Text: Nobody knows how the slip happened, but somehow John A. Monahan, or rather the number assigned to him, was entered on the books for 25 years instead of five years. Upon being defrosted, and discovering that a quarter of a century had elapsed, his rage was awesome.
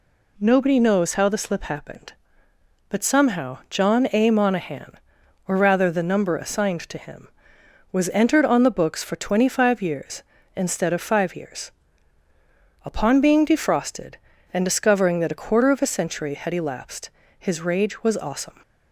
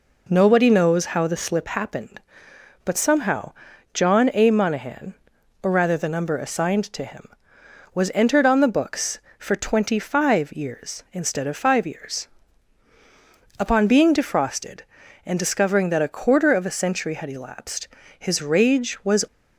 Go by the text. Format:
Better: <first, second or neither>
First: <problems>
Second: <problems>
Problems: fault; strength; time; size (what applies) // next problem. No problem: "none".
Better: first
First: none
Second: pauses between "somehow" and "John"; at 3.5 s; 0.40 s long // stops before "awesome"; at 19.2 s